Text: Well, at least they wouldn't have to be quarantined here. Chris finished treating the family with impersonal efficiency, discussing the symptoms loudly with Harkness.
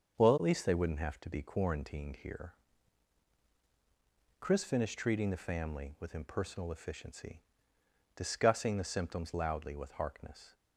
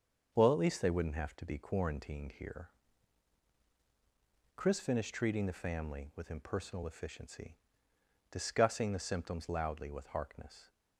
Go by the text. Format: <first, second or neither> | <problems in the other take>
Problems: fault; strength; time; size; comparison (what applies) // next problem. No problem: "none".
neither | starts louder than the rest; the same in both